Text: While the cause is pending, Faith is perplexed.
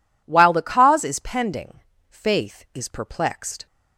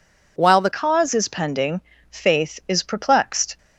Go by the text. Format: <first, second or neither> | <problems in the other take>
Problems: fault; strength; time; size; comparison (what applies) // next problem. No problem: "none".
first | changes voice at "cause"; from 0.7 s on; 2.8 s long